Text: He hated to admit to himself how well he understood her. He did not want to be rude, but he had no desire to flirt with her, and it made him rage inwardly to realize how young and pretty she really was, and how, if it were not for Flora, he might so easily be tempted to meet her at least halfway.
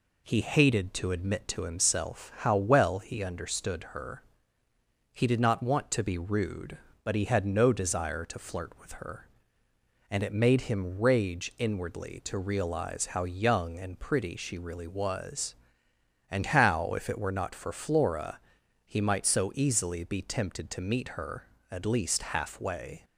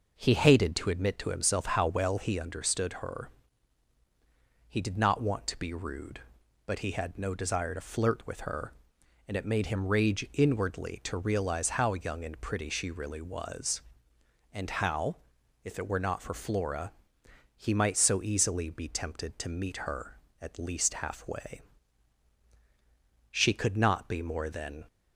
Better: first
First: none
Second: goes on to say "She could not be more than"; from 23.3 s on; 1.5 s long

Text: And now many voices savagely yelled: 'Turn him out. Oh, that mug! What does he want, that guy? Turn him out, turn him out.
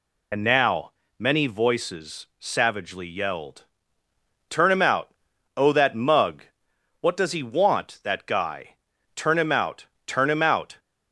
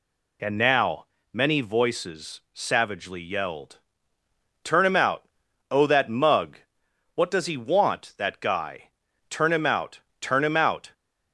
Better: second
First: loses the start of "And"; at 0.3 s; 60 ms // pauses between "now" and "many"; slight; at 0.9 s; 0.30 s long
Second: pauses between "now" and "many"; slight; at 1.0 s; 0.30 s long

